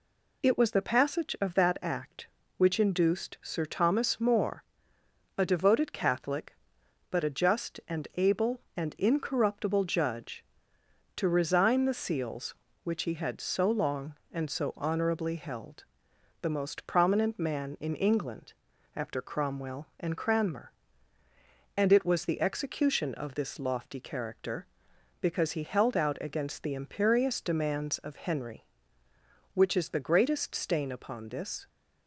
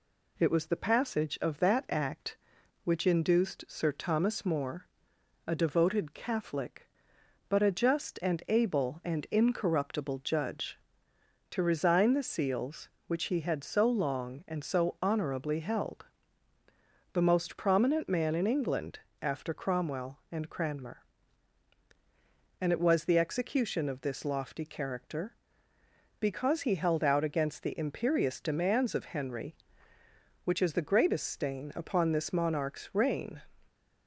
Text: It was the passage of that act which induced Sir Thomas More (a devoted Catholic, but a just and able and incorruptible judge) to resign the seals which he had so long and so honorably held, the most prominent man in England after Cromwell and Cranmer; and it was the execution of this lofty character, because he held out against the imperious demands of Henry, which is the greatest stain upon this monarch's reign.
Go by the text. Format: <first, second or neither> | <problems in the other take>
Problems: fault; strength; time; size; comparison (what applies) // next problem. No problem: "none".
second | pauses between "England" and "after"; at 18.5 s; 0.40 s long; slight in the second // stops before "monarch's reign"; at 31.6 s